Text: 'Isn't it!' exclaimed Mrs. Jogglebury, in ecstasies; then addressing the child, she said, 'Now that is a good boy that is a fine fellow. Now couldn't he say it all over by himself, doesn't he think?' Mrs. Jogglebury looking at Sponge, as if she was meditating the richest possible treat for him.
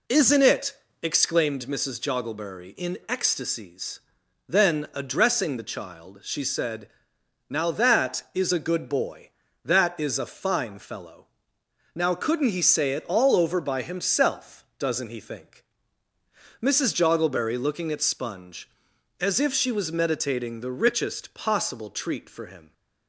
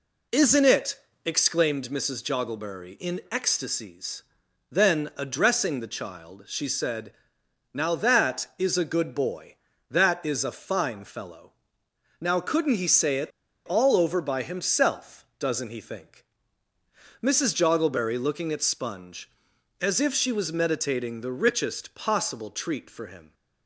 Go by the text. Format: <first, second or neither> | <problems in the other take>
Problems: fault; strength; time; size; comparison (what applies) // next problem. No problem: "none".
first | pauses between "it" and "all"; at 13.3 s; 0.36 s long